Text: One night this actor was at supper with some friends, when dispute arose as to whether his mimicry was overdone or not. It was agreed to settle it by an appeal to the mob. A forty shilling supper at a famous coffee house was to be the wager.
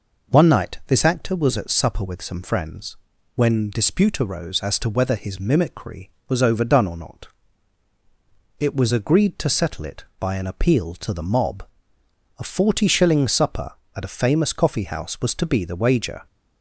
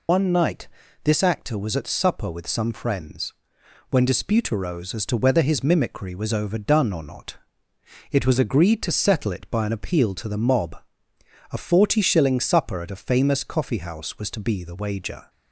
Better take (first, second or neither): first